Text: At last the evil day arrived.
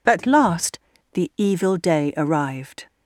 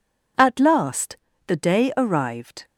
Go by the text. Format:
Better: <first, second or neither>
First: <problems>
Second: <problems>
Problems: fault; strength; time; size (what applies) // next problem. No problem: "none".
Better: first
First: pauses between "last" and "the"; slight; at 0.7 s; 0.36 s long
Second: pauses between "last" and "the"; slight; at 1.1 s; 0.32 s long // skips "evil"; at 1.5 s